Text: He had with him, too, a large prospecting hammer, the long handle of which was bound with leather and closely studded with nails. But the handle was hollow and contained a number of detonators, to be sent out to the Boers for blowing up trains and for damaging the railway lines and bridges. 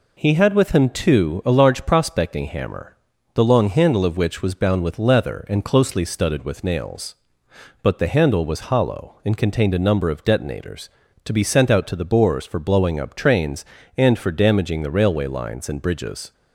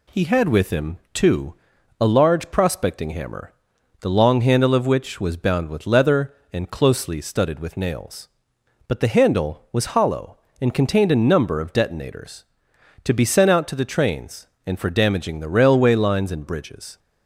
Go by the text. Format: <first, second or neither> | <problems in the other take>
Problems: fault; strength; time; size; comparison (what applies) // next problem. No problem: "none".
first | skips "Boers for blowing up"; at 13.8 s